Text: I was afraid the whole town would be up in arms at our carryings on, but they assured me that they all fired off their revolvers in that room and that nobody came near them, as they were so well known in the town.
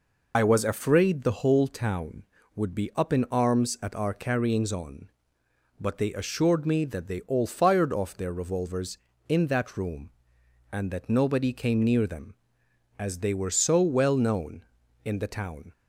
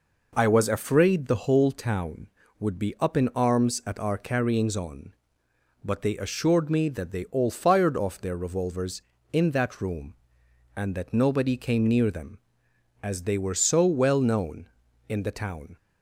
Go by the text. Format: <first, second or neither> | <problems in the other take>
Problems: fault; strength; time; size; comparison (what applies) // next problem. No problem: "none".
second | loses the start of "I"; at 0.3 s; 60 ms